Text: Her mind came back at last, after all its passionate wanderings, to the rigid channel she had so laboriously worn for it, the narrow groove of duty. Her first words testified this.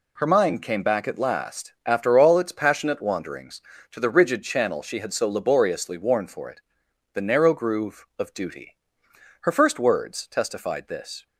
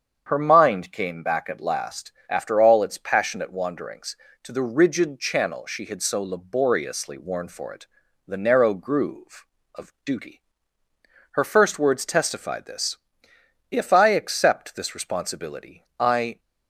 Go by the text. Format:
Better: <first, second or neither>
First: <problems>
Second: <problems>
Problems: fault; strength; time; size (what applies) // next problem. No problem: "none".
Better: first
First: none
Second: starts louder than the rest; strong; until 1.2 s; 7 dB // goes on to say "If I accept this responsibility I"; strong; from 13.7 s on; 2.6 s long